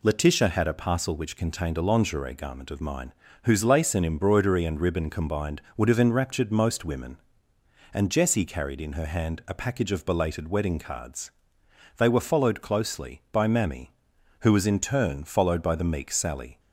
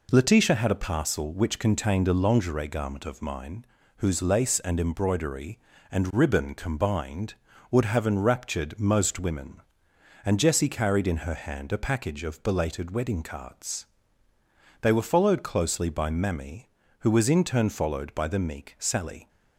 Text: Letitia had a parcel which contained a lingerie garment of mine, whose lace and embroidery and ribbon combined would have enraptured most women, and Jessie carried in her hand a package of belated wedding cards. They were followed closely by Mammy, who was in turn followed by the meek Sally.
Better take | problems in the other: neither | none

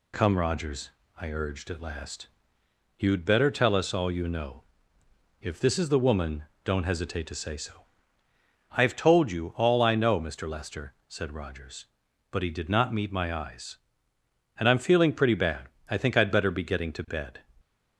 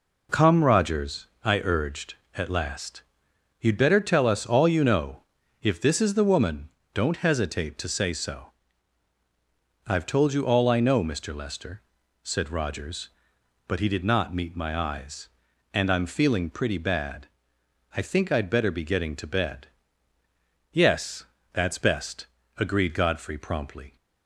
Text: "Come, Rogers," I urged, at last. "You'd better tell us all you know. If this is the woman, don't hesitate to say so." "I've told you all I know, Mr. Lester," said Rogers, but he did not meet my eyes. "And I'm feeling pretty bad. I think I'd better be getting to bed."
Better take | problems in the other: first | goes on to say "Yes that's best agreed Godfrey promptly"; strong; from 20.7 s on; 3.2 s long

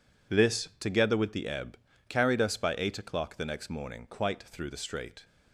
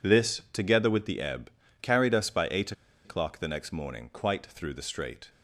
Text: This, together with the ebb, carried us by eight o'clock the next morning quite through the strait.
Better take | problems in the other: first | pauses between "eight" and "o'clock"; slight; at 2.7 s; 0.32 s long

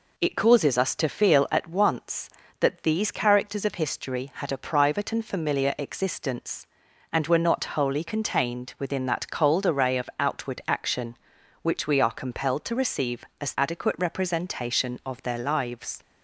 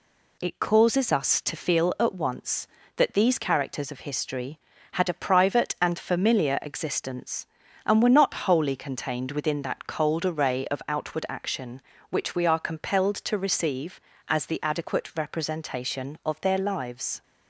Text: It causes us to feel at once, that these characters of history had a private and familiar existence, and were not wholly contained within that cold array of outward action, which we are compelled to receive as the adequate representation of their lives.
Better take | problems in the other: second | skips "the"; at 13.5 s

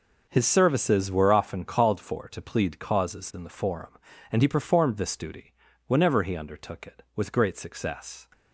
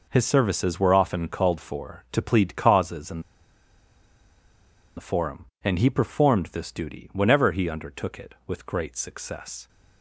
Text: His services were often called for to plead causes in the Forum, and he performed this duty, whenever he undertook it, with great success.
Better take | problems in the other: first | pauses between "in" and "the"; strong; at 3.1 s; 1.7 s long

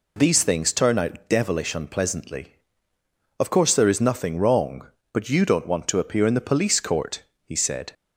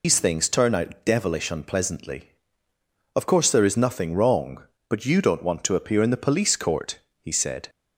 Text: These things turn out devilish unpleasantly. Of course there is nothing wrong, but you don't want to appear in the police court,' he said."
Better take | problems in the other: first | loses the start of "These"; at 0.0 s; 125 ms

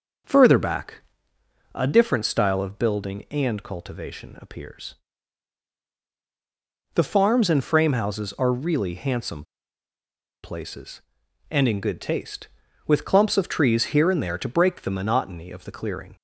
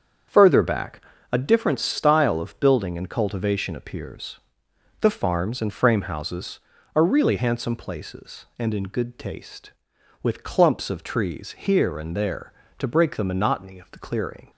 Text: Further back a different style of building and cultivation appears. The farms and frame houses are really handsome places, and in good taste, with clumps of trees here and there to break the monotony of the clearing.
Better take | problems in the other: second | starts louder than the rest; until 2.0 s; 6.5 dB; strong in the second // pauses between "back" and "a"; noticeable; at 1.0 s; 0.76 s long; slight in the second // pauses between "handsome" and "places"; at 9.4 s; 0.99 s long

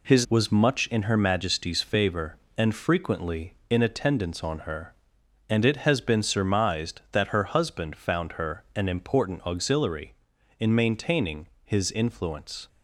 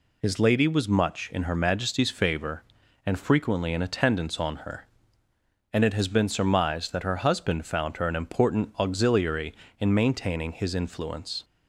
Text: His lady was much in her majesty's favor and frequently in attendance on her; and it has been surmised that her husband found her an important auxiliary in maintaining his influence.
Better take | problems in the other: second | skips "lady"; at 0.2 s // pauses between "maintaining" and "his"; slight; at 11.4 s; 0.16 s long

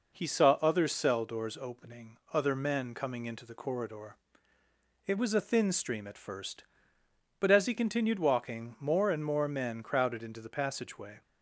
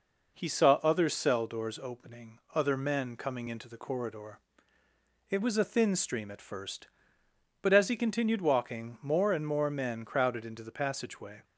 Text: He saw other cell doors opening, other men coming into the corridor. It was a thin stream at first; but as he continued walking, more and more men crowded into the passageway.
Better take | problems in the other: neither | none

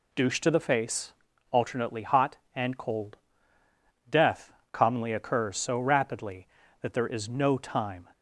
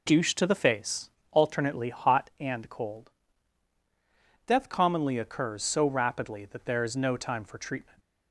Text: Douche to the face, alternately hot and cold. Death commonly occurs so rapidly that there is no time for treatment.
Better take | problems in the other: second | pauses between "Death" and "commonly"; slight; at 4.5 s; 0.22 s long // stops before "for treatment"; at 8.1 s

